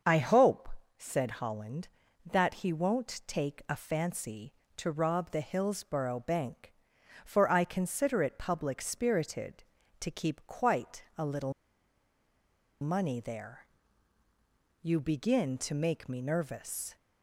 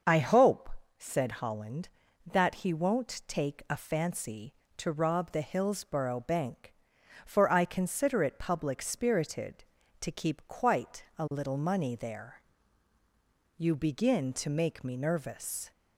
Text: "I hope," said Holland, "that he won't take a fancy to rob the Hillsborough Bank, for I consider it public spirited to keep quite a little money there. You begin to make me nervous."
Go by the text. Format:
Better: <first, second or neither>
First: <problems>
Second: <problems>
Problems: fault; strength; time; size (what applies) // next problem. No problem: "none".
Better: second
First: starts louder than the rest; until 1.3 s; 6.5 dB // pauses between "quite" and "a"; slight; at 11.0 s; 0.16 s long // pauses between "little" and "money"; strong; at 11.5 s; 1.2 s long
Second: starts louder than the rest; until 1.3 s; 6.5 dB // pauses between "quite" and "a"; slight; at 11.0 s; 0.16 s long